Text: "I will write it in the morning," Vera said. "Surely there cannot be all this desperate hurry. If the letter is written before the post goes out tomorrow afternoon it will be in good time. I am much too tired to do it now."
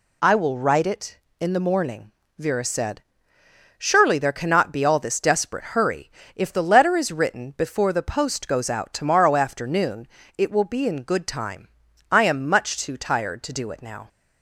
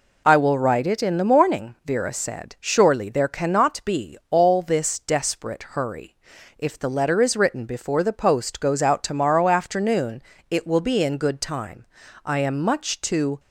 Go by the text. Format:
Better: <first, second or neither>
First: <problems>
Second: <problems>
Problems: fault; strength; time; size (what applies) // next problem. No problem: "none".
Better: first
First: pauses between "afternoon" and "it"; slight; at 10.0 s; 0.30 s long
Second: pauses between "afternoon" and "it"; slight; at 10.2 s; 0.28 s long // stops before "tired to do it now"; at 13.3 s